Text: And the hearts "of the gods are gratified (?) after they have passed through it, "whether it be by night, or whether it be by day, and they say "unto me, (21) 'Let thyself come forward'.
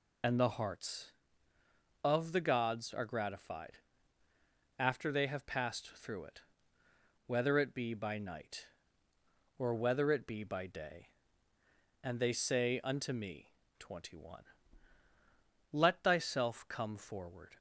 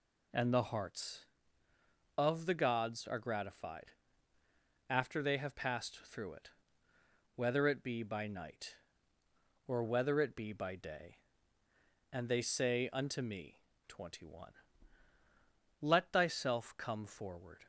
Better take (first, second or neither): second